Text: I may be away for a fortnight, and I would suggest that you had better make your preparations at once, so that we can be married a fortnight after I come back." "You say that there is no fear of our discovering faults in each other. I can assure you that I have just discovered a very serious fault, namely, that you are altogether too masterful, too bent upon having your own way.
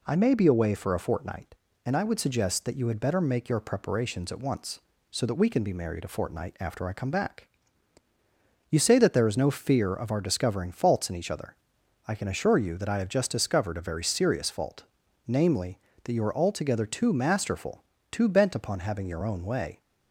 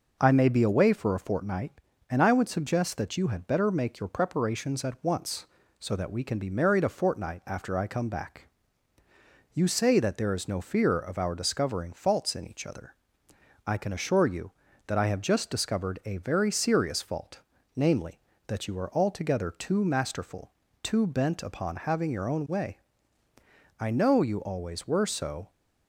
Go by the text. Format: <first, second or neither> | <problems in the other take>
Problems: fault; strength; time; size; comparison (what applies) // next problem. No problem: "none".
first | goes on to say "I know you always were so"; strong; from 23.7 s on; 1.7 s long